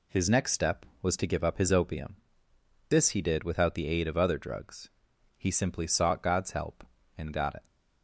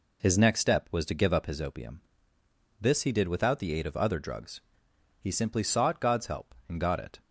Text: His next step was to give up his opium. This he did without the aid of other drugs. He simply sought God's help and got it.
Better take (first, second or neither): neither